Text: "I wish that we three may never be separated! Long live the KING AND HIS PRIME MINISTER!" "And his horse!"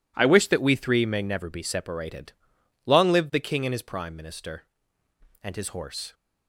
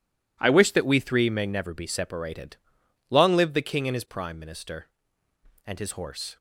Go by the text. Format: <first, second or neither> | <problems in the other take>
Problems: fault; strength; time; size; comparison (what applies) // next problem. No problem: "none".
neither | none